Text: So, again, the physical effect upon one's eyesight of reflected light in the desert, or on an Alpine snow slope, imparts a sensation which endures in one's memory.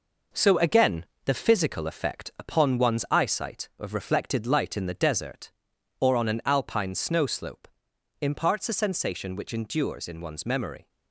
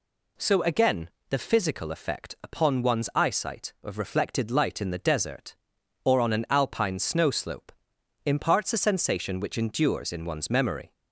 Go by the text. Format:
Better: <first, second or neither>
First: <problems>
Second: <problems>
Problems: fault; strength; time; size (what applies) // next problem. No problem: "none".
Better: second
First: gets quieter; noticeable; throughout; 6 dB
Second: none